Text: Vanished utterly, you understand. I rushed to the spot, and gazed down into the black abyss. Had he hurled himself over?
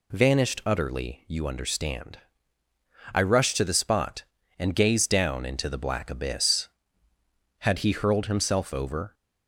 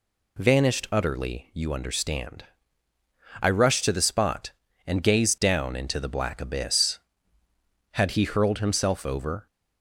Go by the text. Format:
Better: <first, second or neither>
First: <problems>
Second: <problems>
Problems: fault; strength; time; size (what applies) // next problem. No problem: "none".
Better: neither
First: none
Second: none